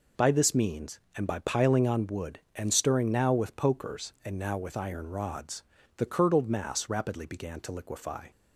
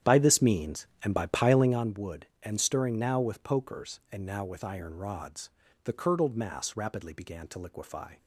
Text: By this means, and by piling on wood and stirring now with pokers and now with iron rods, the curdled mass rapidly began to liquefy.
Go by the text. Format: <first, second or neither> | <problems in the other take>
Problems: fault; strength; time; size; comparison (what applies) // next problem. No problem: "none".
first | starts louder than the rest; strong; until 1.8 s; 10 dB